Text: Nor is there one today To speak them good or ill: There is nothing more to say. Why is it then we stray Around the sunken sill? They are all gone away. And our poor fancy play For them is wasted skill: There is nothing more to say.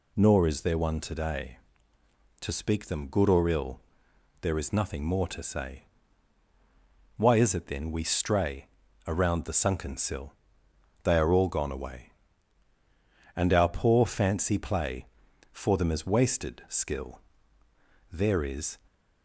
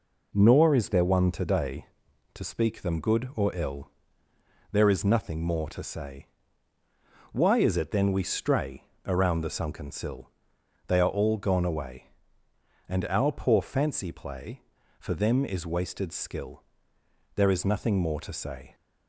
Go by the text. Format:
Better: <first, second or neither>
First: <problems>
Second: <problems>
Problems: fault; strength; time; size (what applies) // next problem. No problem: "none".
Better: second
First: pauses between "stray" and "Around"; at 8.6 s; 0.38 s long // stops before "nothing more to say"; at 18.8 s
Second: pauses between "stray" and "Around"; slight; at 8.8 s; 0.24 s long